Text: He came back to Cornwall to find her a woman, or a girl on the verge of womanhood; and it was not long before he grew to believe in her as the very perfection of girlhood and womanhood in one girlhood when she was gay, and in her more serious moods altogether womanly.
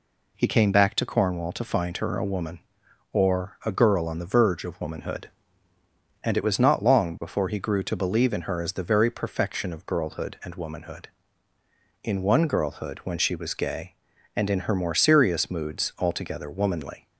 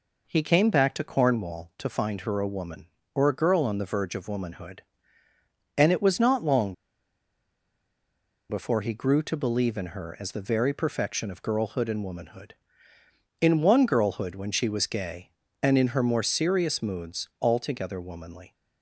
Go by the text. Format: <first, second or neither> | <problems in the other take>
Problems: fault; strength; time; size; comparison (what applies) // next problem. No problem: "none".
first | pauses between "long" and "before"; strong; at 6.7 s; 1.7 s long